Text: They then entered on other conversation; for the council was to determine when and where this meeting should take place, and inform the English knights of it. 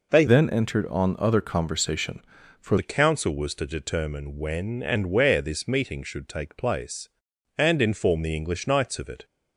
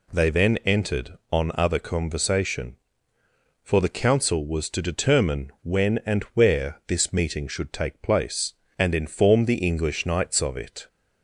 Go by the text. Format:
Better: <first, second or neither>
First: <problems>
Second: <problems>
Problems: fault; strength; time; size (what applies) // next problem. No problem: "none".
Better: second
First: changes voice from "then" to "for"; from 0.2 to 2.7 s; 2.5 s long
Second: none